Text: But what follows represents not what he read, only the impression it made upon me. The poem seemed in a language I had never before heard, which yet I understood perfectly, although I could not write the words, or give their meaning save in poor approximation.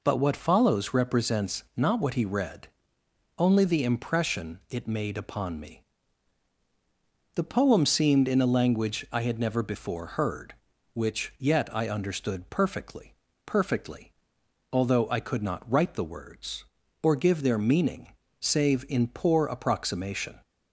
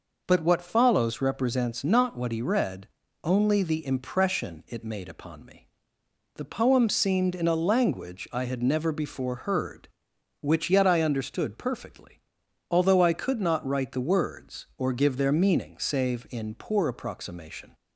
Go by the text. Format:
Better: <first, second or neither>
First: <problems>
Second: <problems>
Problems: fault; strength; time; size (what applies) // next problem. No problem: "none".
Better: second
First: says "perfectly" twice; at 13.4 s // pauses between "meaning" and "save"; slight; at 18.1 s; 0.26 s long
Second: none